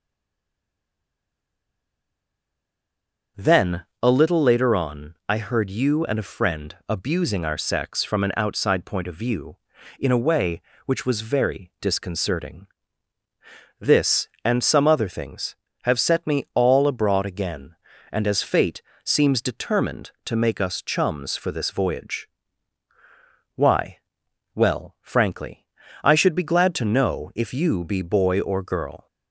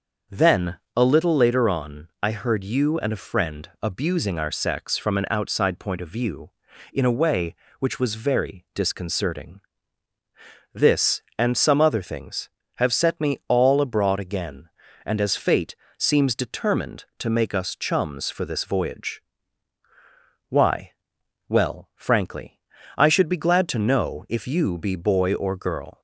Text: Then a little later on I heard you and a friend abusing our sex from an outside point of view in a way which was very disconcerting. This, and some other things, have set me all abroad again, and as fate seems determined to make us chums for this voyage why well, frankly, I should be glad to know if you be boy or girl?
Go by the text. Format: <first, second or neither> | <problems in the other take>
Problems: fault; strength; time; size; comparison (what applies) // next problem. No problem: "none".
second | stays silent before the first word; strong; until 3.3 s; 3.3 s long // starts louder than the rest; until 4.5 s; 6.5 dB; also in the second // pauses between "Then" and "a"; slight; at 3.8 s; 0.20 s long; slight in the second // pauses between "fate" and "seems"; slight; at 18.8 s; 0.22 s long; slight in the second // pauses between "voyage" and "why"; strong; at 22.2 s; 1.2 s long; strong in the second // pauses between "why" and "well"; noticeable; at 23.9 s; 0.56 s long; noticeable in the second